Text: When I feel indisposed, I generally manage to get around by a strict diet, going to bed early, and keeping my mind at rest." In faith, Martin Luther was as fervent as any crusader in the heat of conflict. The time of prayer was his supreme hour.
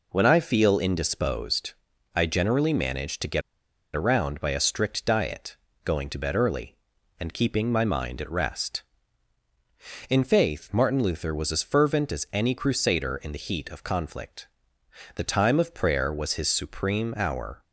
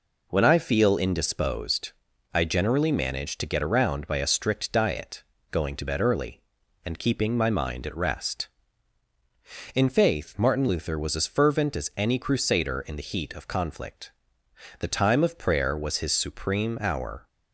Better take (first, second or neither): second